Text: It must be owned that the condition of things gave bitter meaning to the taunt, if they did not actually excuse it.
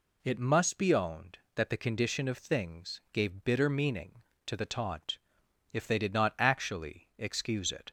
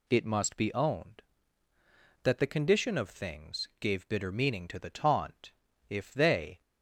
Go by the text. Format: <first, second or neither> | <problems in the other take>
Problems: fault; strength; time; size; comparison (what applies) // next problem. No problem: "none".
first | stops before "did not actually excuse it"; at 6.6 s